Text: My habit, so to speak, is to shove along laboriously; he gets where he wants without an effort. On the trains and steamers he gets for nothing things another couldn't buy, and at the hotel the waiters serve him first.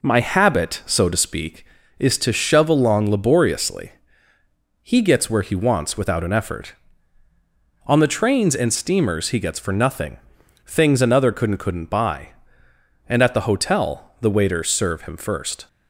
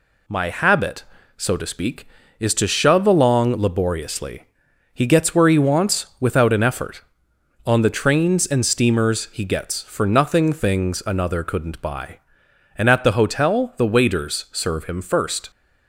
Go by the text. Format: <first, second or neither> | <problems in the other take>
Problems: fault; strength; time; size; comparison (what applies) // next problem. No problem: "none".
second | pauses between "nothing" and "things"; noticeable; at 10.1 s; 0.48 s long // says "couldn't" twice; at 11.5 s